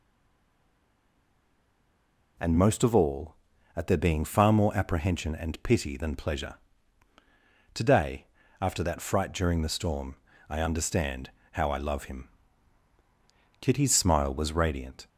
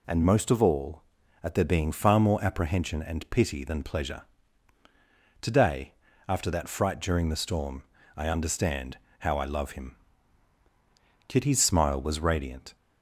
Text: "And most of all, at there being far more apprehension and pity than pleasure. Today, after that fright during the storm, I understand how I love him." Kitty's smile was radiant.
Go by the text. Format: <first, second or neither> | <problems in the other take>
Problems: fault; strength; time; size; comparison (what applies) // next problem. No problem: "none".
second | stays silent before the first word; until 2.3 s; 2.3 s long // pauses between "understand" and "how"; slight; at 11.3 s; 0.22 s long; slight in the second